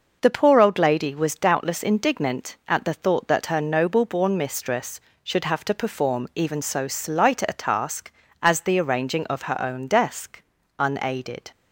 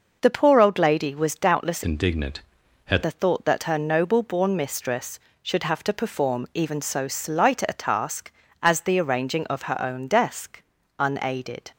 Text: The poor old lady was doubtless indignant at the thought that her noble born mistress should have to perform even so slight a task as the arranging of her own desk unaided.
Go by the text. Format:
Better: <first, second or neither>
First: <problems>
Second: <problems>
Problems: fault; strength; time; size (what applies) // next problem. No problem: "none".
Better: first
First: pauses between "desk" and "unaided"; at 10.4 s; 0.38 s long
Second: changes voice from "indignant" to "at"; from 1.8 to 3.0 s; 1.2 s long // pauses between "desk" and "unaided"; at 10.6 s; 0.38 s long